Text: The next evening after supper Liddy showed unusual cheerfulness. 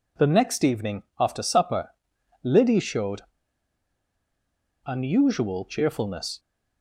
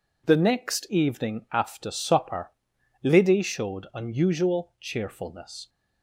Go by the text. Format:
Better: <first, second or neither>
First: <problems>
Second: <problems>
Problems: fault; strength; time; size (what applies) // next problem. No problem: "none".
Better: second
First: pauses between "evening" and "after"; slight; at 1.0 s; 0.18 s long // pauses between "supper" and "Liddy"; noticeable; at 1.8 s; 0.52 s long // pauses between "showed" and "unusual"; strong; at 3.1 s; 1.6 s long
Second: pauses between "supper" and "Liddy"; noticeable; at 2.5 s; 0.52 s long